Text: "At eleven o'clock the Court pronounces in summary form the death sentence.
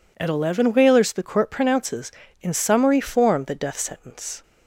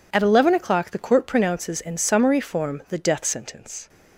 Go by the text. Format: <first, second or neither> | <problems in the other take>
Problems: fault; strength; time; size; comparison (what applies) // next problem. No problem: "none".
second | says "whalers" for "o'clock"; at 0.7 s